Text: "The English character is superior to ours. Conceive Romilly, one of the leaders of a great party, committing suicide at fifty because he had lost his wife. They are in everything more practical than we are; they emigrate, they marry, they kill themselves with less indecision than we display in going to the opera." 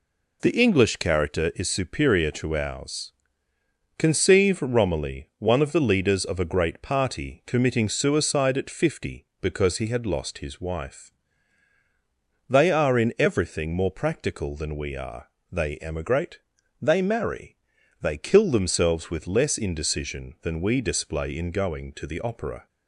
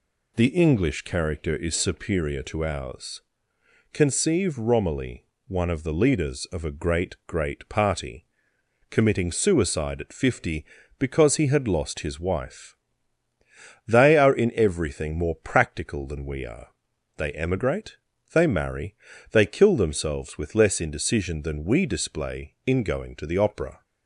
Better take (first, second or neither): first